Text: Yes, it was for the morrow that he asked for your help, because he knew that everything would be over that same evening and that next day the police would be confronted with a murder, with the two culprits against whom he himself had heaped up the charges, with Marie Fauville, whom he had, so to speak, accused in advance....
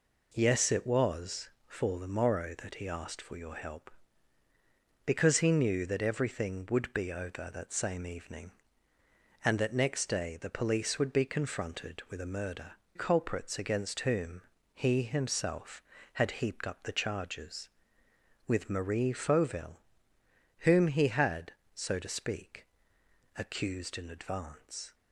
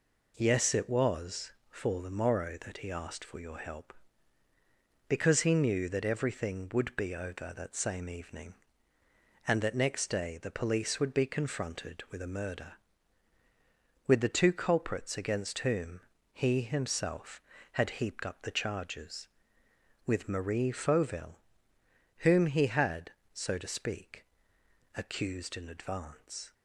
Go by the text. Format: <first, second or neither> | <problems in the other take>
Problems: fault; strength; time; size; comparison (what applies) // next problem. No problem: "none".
second | skips "with the two"; at 12.8 s // pauses between "whom" and "he"; slight; at 14.4 s; 0.32 s long; slight in the second